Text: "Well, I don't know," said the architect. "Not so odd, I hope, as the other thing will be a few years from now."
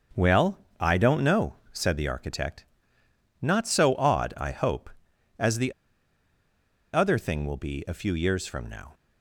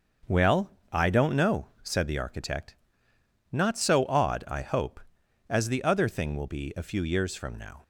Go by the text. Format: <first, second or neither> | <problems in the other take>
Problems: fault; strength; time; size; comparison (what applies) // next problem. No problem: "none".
second | starts louder than the rest; until 1.3 s; 6.5 dB; also in the second // pauses between "the" and "other"; at 5.7 s; 1.2 s long